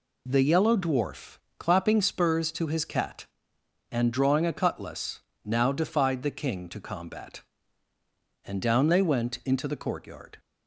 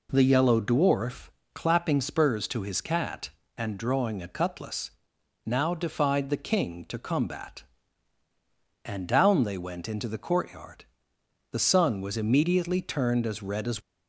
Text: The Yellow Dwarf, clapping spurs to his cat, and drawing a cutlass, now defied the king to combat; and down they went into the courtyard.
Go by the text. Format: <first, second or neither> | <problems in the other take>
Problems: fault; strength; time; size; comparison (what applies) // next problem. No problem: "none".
first | goes on to say "The sun was immediately turned as red as"; strong; from 11.5 s on; 2.2 s long